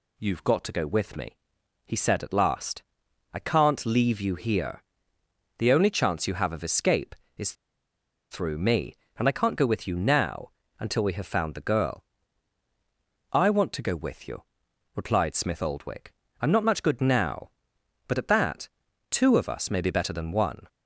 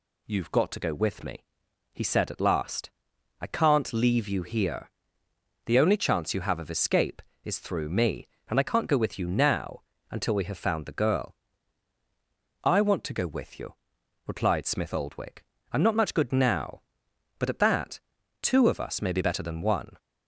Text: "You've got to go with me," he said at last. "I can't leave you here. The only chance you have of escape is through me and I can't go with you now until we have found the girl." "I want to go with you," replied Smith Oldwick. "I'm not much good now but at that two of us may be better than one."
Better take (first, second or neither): second